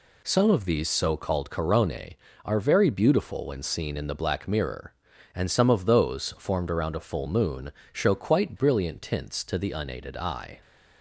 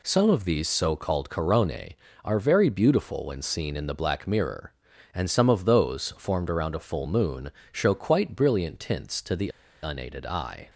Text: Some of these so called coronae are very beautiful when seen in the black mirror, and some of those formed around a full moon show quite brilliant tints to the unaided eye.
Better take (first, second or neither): first